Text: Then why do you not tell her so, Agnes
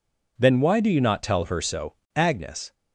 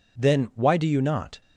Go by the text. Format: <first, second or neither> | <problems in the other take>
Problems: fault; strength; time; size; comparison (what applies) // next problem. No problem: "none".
first | stops before "tell her so Agnes"; at 1.4 s